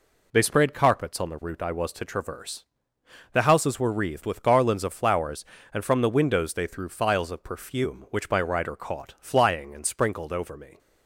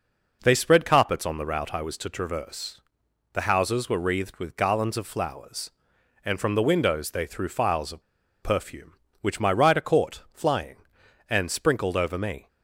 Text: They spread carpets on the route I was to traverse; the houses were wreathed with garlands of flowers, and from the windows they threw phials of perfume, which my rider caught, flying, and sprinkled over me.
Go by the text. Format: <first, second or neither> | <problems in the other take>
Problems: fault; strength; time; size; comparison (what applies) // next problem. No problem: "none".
first | pauses between "of" and "perfume"; at 8.0 s; 0.40 s long